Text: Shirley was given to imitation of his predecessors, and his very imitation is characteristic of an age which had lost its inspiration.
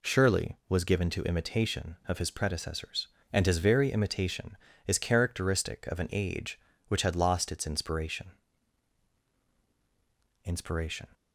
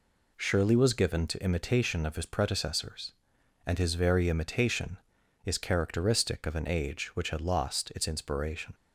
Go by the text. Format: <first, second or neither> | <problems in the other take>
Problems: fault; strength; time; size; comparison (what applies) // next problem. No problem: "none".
second | says "inspiration" twice; at 10.4 s